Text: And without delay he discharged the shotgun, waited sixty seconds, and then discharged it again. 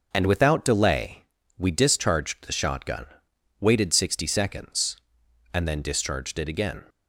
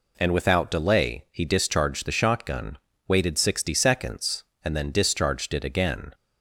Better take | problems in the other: second | starts louder than the rest; until 1.1 s; 6.5 dB // says "we" for "he"; at 1.5 s

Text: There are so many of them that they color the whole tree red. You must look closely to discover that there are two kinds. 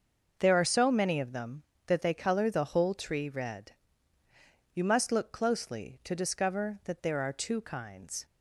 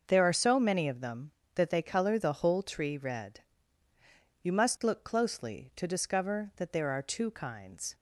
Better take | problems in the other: neither | starts louder than the rest; noticeable; the same in both

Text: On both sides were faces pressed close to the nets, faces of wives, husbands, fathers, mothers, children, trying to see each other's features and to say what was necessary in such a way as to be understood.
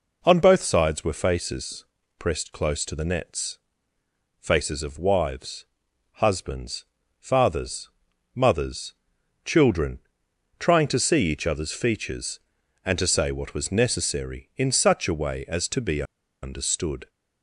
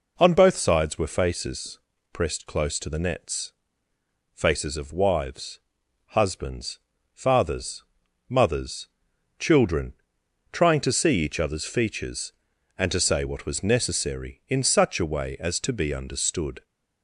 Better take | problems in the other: second | pauses between "faces" and "pressed"; slight; at 1.8 s; 0.36 s long; slight in the second // pauses between "be" and "understood"; at 16.0 s; 0.38 s long

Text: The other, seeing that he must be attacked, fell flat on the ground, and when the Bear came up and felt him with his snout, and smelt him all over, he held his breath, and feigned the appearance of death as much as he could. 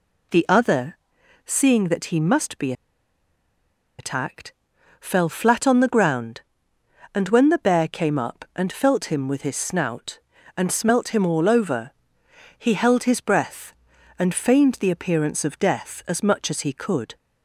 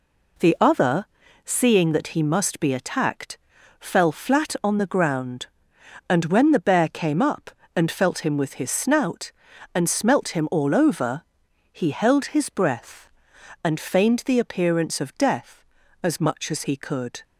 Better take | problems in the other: second | pauses between "be" and "attacked"; strong; at 2.7 s; 1.2 s long

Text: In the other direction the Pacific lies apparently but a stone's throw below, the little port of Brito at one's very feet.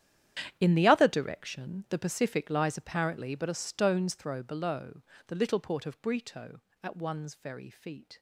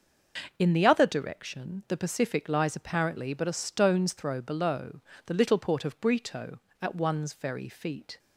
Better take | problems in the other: second | gets quieter; strong; throughout; 16.5 dB // starts louder than the rest; strong; until 1.6 s; 10.5 dB; noticeable in the second

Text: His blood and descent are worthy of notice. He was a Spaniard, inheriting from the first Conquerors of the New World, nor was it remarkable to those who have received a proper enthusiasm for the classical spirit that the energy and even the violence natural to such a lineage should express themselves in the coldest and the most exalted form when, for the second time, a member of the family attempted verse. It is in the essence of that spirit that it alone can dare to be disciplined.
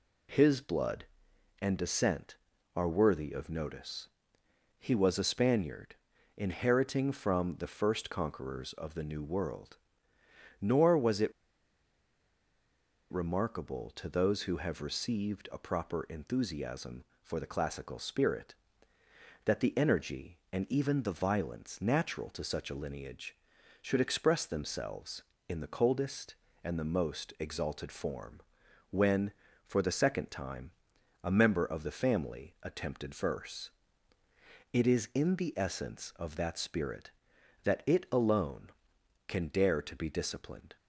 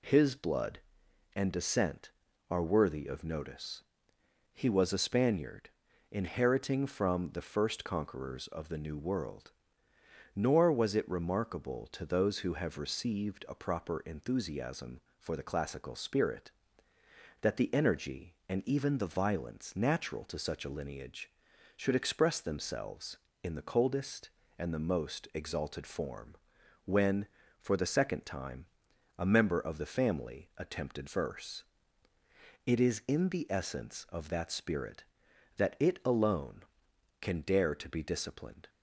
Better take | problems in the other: second | pauses between "it" and "remarkable"; strong; at 11.3 s; 1.7 s long // pauses between "form" and "when"; noticeable; at 28.3 s; 0.52 s long; noticeable in the second

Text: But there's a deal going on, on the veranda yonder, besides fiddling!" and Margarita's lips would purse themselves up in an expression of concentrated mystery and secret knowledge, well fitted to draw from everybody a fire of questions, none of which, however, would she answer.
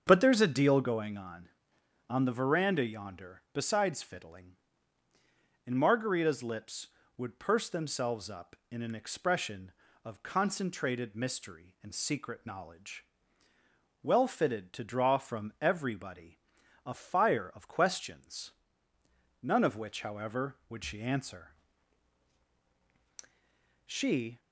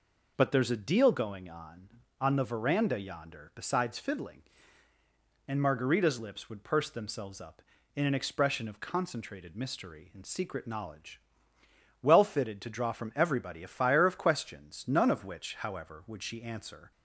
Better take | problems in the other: second | starts louder than the rest; until 1.0 s; 7 dB // pauses between "everybody" and "a"; noticeable; at 16.3 s; 0.48 s long // goes on to say "She"; from 23.8 s on; 0.54 s long

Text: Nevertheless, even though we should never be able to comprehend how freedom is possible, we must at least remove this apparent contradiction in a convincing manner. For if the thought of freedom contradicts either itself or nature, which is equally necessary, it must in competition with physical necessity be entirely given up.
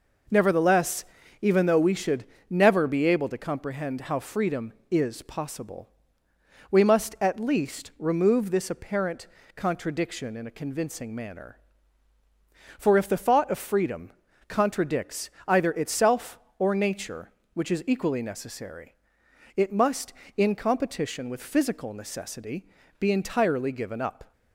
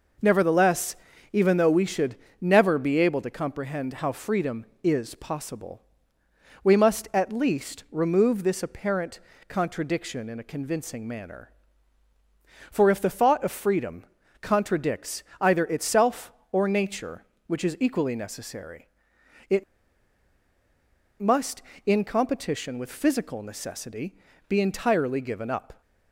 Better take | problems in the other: first | pauses between "should" and "never"; slight; at 2.1 s; 0.26 s long; slight in the first // pauses between "apparent" and "contradiction"; slight; at 9.1 s; 0.28 s long; slight in the first // pauses between "freedom" and "contradicts"; slight; at 14.0 s; 0.36 s long; slight in the first // pauses between "contradicts" and "either"; slight; at 15.2 s; 0.16 s long; slight in the first // pauses between "it" and "must"; strong; at 19.6 s; 1.5 s long // pauses between "necessity" and "be"; slight; at 24.1 s; 0.32 s long; slight in the first

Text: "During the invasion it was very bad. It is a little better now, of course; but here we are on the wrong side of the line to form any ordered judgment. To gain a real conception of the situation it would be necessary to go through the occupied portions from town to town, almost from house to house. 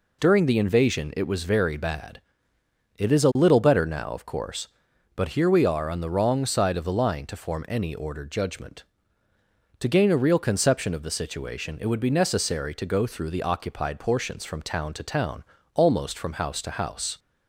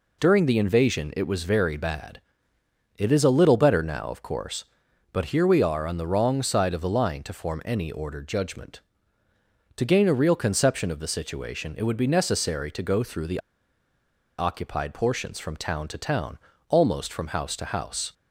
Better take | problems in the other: first | pauses between "the" and "occupied"; at 13.3 s; 0.98 s long

